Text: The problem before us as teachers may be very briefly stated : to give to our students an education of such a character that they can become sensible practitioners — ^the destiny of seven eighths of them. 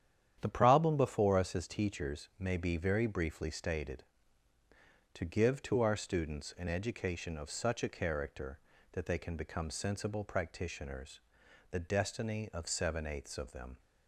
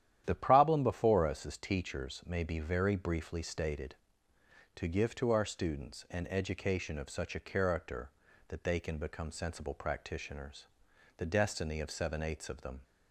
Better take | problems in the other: neither | starts louder than the rest; strong; the same in both

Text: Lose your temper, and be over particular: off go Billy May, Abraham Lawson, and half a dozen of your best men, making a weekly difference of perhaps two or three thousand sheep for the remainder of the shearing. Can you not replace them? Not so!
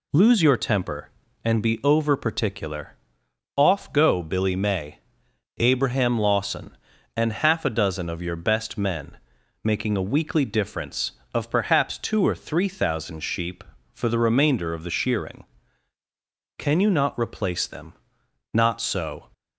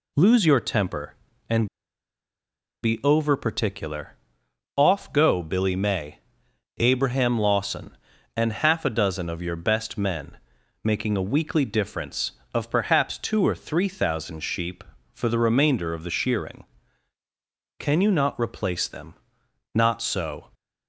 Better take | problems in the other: first | pauses between "and" and "be"; at 1.6 s; 1.1 s long

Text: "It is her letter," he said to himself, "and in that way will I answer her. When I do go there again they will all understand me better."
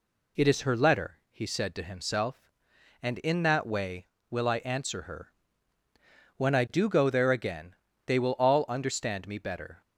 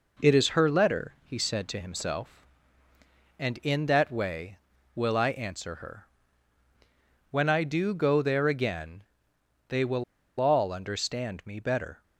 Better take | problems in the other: first | pauses between "again" and "they"; noticeable; at 9.0 s; 0.66 s long; slight in the first // pauses between "will" and "all"; at 10.0 s; 0.36 s long

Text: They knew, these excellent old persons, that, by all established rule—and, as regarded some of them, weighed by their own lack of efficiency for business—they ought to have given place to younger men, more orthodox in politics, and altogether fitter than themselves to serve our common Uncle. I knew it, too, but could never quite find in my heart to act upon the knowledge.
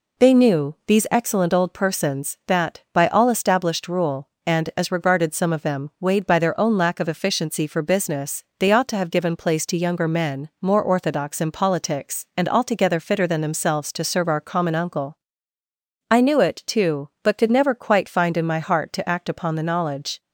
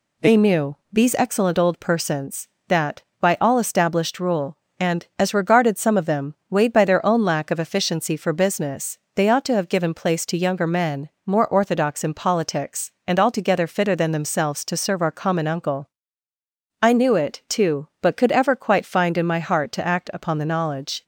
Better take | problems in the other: first | says "ever" for "never"; at 18.3 s

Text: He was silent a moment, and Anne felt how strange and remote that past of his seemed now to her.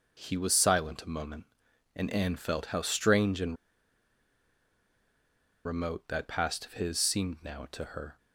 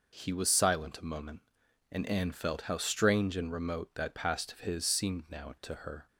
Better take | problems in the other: second | pauses between "and" and "remote"; strong; at 3.5 s; 2.0 s long

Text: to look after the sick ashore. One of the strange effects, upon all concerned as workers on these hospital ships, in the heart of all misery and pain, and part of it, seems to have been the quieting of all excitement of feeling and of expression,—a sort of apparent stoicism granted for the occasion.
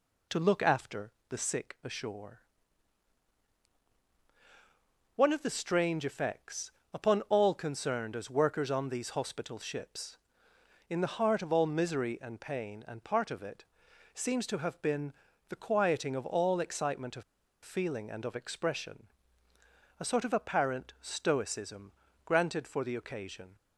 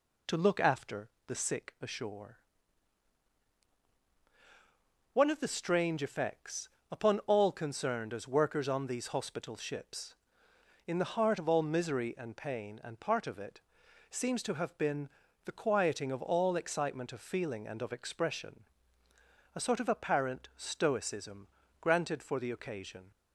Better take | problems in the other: second | pauses between "after" and "the"; slight; at 1.0 s; 0.20 s long; slight in the second // pauses between "been" and "the"; slight; at 15.1 s; 0.36 s long; slight in the second // pauses between "of" and "feeling"; at 17.2 s; 0.40 s long // pauses between "stoicism" and "granted"; slight; at 21.9 s; 0.34 s long; slight in the second

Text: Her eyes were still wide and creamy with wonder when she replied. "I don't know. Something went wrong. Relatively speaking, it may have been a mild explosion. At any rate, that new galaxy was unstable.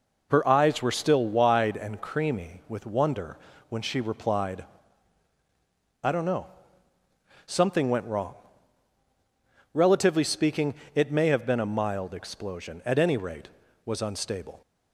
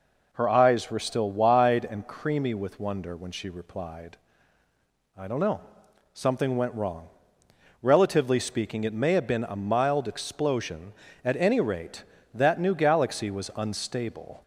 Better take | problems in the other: second | pauses between "wonder" and "when"; slight; at 3.3 s; 0.32 s long // skips "that new galaxy"; at 13.6 s

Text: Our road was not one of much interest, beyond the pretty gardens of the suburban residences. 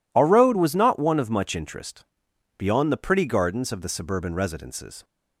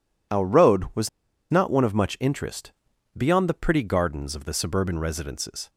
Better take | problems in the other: first | pauses between "was" and "not"; at 1.0 s; 0.42 s long

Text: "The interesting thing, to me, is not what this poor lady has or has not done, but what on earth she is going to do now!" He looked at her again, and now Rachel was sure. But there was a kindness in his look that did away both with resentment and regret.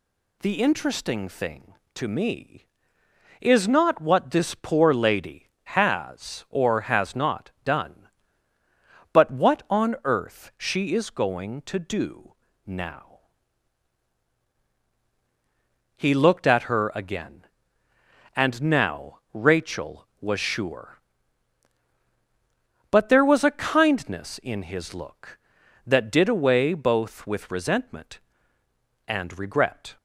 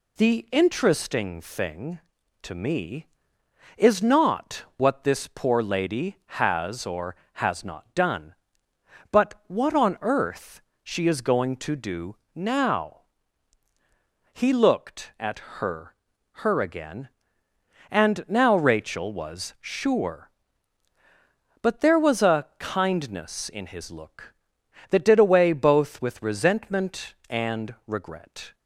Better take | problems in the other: first | pauses between "earth" and "she"; slight; at 10.6 s; 0.22 s long // pauses between "do" and "now"; slight; at 12.1 s; 0.20 s long; slight in the first // pauses between "at" and "her"; slight; at 15.3 s; 0.18 s long // says "her" twice; at 16.3 s

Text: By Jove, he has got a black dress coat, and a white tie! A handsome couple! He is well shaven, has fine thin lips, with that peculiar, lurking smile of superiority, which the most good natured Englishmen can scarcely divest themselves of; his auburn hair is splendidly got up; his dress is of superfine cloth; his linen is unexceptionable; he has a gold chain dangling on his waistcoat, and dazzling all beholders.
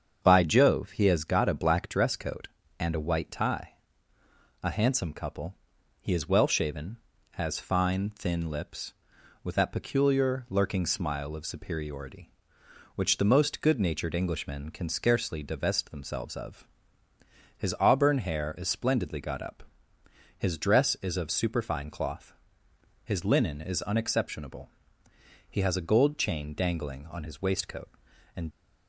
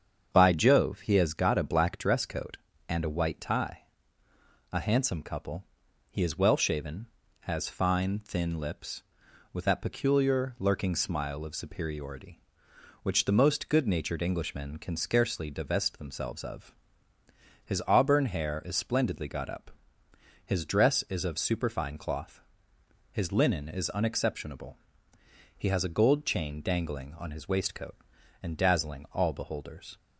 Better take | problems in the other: second | starts louder than the rest; strong; until 1.2 s; 7.5 dB; strong in the second // stops before "dazzling all beholders"; at 28.5 s

